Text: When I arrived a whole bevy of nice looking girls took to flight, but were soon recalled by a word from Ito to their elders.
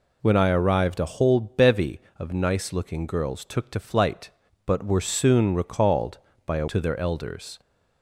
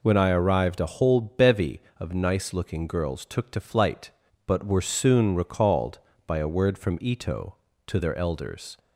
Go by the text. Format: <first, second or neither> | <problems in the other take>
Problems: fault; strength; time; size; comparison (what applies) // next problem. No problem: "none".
second | skips "word from Ito"; at 6.6 s